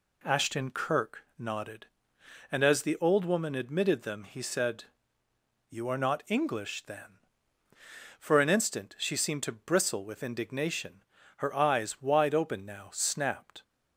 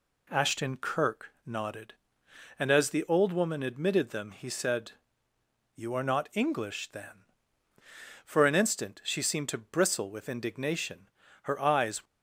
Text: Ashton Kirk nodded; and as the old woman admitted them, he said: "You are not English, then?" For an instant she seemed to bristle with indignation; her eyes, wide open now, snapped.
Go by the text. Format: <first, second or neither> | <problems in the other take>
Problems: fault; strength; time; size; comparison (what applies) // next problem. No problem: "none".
first | stops before "wide open now snapped"; at 12.0 s